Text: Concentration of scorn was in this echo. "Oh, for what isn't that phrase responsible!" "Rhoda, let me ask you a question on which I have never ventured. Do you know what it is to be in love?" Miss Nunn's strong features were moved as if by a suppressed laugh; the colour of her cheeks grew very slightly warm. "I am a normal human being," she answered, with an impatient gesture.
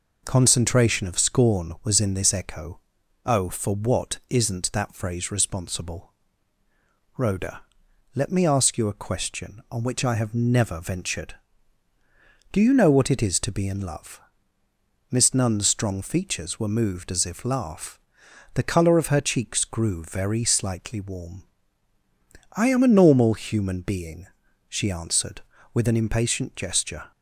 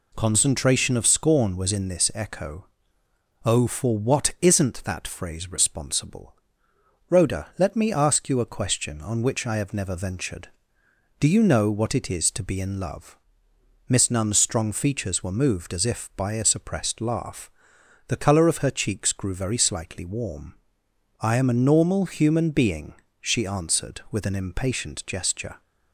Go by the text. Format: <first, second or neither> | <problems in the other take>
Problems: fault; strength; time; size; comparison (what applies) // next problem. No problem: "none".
second | skips "by a suppressed"; at 17.4 s